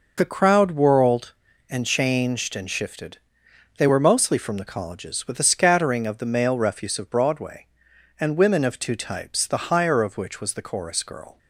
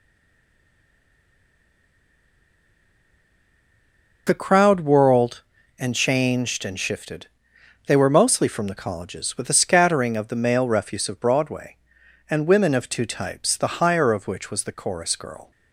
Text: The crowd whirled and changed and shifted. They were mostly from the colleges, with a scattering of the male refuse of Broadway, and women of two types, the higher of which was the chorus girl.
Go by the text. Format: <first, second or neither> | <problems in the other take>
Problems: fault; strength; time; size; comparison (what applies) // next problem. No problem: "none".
first | stays silent before the first word; strong; until 4.2 s; 4.2 s long